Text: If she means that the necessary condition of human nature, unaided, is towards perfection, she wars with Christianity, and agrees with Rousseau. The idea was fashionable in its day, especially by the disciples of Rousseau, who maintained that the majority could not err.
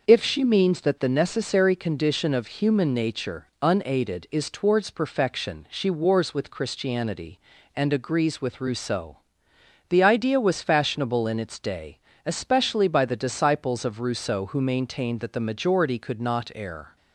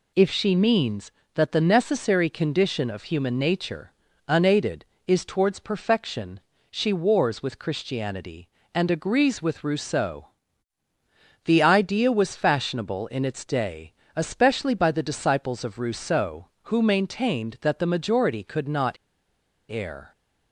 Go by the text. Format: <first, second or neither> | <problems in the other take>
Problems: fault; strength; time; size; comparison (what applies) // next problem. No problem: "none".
first | pauses between "not" and "err"; noticeable; at 18.9 s; 0.74 s long